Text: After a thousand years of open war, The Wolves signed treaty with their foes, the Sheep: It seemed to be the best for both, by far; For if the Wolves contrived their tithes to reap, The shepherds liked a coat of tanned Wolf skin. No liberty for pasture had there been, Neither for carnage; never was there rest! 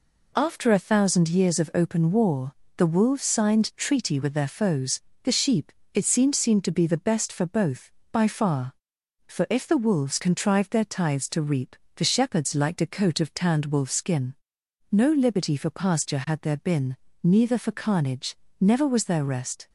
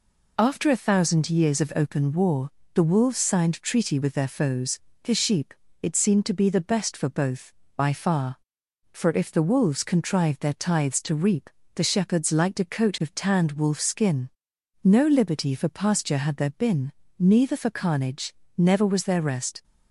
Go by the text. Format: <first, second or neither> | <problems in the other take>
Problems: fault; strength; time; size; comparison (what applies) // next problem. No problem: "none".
second | says "seemed" twice; at 6.3 s